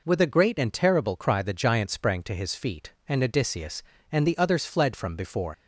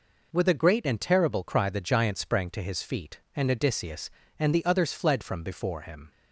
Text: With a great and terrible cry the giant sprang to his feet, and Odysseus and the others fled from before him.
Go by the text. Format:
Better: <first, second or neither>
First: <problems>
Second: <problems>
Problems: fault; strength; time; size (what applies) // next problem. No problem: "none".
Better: second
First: stops before "him"; at 5.5 s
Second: none